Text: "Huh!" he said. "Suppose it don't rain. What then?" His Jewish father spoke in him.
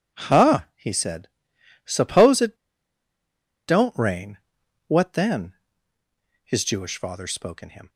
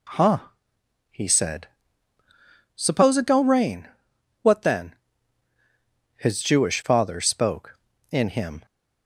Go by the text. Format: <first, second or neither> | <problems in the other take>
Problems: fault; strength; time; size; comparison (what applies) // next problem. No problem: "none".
second | pauses between "it" and "don't"; at 2.5 s; 1.1 s long